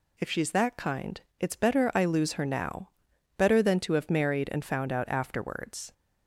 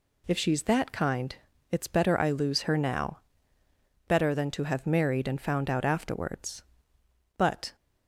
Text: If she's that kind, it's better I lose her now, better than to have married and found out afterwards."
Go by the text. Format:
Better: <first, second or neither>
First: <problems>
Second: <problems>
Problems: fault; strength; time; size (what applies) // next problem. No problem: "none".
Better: first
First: none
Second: goes on to say "But"; slight; from 7.3 s on; 0.38 s long